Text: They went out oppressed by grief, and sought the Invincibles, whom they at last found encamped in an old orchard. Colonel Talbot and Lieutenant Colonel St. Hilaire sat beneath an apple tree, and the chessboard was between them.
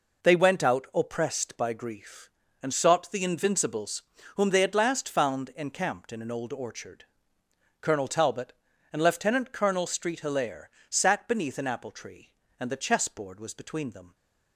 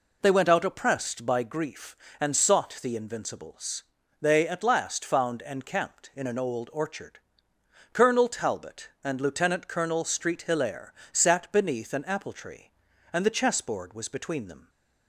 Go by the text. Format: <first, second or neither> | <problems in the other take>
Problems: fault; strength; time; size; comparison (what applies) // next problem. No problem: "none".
first | skips "whom"; at 4.0 s // pauses between "Hilaire" and "sat"; slight; at 10.9 s; 0.18 s long; slight in the first